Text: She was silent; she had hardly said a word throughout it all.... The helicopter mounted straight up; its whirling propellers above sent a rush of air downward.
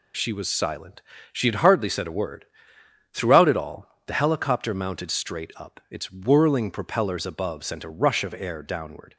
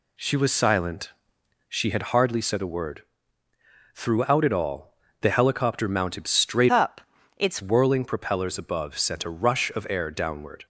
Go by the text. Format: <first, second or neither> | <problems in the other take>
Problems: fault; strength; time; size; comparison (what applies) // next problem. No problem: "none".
first | pauses between "word" and "throughout"; noticeable; at 3.0 s; 0.92 s long; noticeable in the first // changes voice from "up" to "its"; from 6.6 to 7.6 s; 1.0 s long